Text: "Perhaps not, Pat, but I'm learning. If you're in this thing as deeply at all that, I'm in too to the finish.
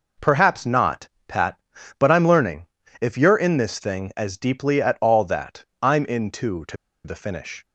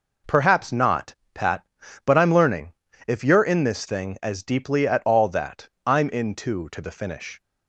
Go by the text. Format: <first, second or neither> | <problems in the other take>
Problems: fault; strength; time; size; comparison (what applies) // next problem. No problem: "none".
second | pauses between "to" and "the"; slight; at 6.7 s; 0.28 s long